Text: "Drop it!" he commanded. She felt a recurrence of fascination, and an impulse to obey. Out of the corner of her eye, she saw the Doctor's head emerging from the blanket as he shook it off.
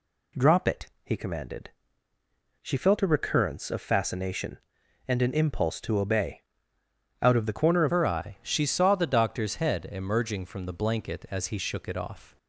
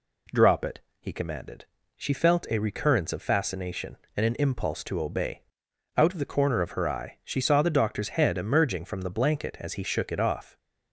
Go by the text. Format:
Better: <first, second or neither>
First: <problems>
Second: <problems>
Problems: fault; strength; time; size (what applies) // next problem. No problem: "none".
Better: second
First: changes voice at "her"; from 7.8 s on; 4.5 s long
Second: none